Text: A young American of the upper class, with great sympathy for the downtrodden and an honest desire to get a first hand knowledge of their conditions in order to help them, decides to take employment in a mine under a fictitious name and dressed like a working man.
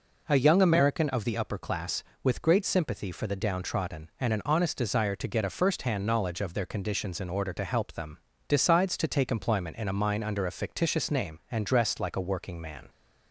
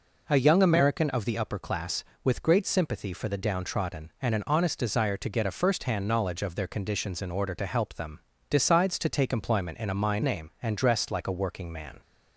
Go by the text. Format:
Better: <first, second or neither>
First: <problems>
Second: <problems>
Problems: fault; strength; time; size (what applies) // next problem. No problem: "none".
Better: first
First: none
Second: skips "under a fictitious"; at 10.2 s